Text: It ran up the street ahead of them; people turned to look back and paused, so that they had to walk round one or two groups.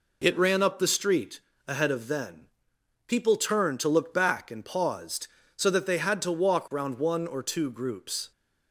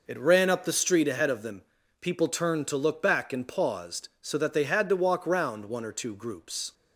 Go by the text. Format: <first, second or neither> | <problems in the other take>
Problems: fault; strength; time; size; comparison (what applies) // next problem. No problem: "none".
second | pauses between "street" and "ahead"; slight; at 1.4 s; 0.26 s long // says "then" for "them"; at 2.0 s